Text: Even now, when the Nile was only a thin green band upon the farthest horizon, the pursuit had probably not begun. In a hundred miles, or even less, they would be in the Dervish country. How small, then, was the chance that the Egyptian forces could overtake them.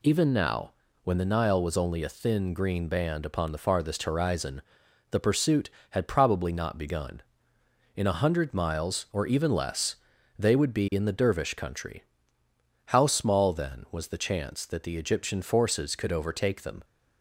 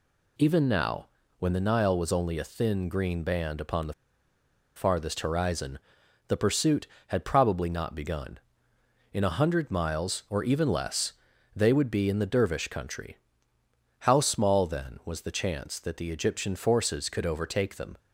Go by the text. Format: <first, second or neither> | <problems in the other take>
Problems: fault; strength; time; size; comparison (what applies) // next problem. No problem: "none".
first | pauses between "the" and "farthest"; noticeable; at 3.9 s; 0.82 s long